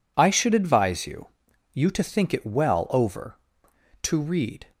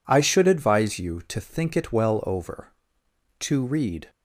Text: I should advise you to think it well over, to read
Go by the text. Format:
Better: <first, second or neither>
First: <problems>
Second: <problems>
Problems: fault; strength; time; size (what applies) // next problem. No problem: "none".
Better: second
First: says "you" twice; at 1.7 s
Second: none